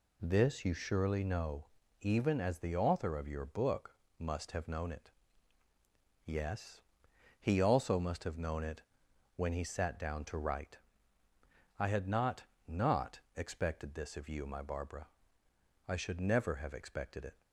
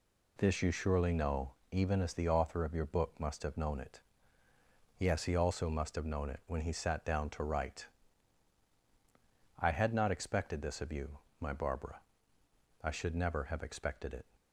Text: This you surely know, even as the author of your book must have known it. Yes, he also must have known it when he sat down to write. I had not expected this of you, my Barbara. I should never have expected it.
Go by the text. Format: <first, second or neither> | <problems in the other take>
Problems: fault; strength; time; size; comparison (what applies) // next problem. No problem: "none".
second | pauses between "book" and "must"; slight; at 3.9 s; 0.24 s long // pauses between "it" and "when"; noticeable; at 8.8 s; 0.54 s long // says "not" twice; at 12.6 s